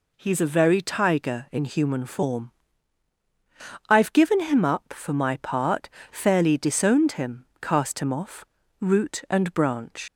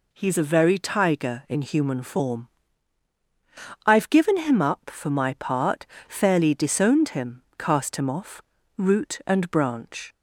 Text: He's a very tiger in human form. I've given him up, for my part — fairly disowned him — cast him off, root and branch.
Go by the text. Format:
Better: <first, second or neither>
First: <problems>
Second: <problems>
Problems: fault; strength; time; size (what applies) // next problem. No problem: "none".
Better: second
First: leaves "branch" unfinished; at 10.0 s; 75 ms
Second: none